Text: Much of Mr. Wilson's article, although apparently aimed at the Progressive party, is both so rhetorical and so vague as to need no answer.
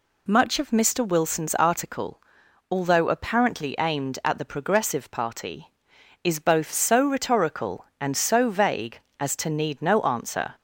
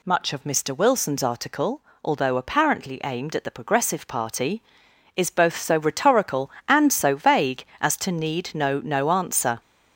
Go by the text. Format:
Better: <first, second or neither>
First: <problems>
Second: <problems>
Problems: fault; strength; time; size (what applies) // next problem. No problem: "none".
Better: first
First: none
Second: says "no" twice; at 8.7 s